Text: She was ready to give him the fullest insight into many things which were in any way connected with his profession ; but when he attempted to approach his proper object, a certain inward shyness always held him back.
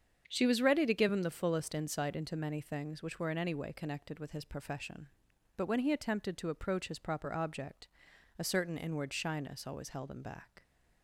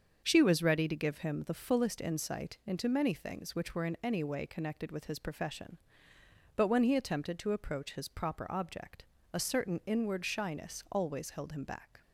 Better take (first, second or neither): neither